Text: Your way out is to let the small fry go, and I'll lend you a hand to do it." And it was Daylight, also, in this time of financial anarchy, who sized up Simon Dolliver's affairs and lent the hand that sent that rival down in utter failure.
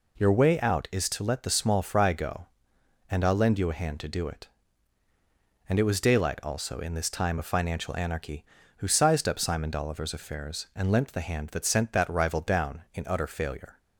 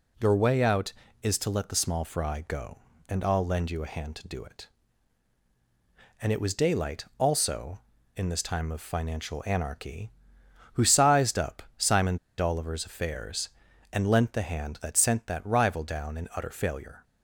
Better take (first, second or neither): first